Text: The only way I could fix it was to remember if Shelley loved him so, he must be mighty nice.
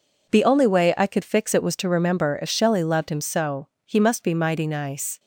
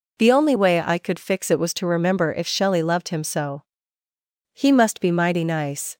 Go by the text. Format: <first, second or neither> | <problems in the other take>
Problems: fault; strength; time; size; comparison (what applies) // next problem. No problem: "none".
neither | none